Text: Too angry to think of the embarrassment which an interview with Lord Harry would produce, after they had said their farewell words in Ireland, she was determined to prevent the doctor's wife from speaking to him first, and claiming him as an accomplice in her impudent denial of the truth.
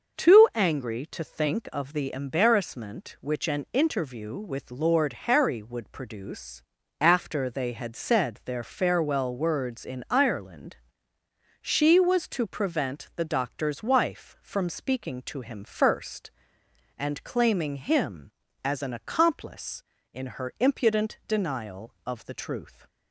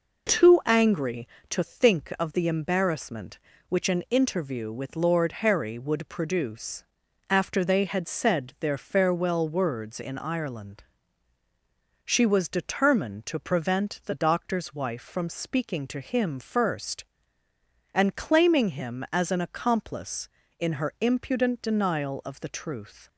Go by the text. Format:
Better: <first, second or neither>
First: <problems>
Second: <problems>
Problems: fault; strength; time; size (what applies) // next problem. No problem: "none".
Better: second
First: starts louder than the rest; noticeable; until 1.2 s; 6 dB // skips "determined"; at 12.2 s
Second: none